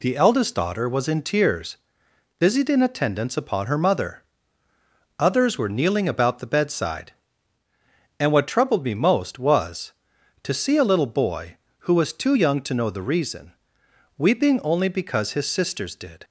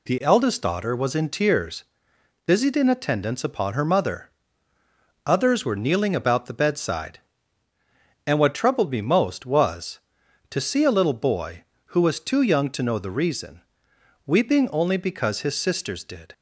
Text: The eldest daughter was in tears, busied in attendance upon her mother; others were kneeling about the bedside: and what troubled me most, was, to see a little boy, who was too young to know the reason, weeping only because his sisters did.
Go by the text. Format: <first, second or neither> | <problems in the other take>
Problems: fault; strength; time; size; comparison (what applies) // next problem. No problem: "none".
neither | none